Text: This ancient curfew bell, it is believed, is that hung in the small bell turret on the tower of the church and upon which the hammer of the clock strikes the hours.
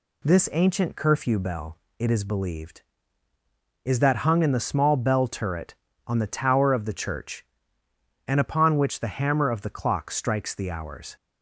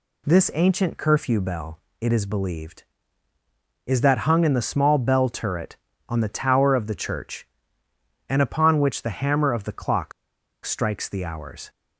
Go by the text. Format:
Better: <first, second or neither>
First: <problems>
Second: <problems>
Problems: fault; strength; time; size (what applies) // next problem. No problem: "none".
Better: first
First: none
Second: pauses between "clock" and "strikes"; noticeable; at 10.1 s; 0.53 s long